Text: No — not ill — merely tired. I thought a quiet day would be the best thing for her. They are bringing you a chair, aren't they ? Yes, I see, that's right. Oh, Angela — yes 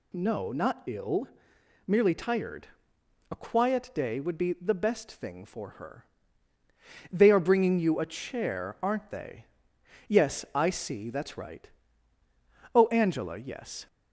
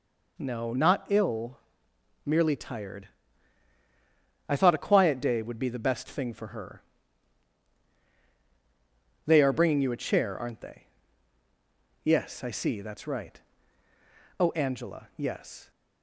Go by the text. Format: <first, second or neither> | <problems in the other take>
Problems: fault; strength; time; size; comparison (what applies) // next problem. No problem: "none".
second | skips "I thought"; at 2.9 s